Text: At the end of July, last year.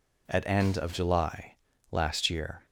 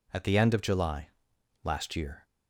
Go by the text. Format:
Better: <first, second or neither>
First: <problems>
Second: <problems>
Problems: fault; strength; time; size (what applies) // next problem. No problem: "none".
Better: second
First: skips "the"; at 0.4 s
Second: none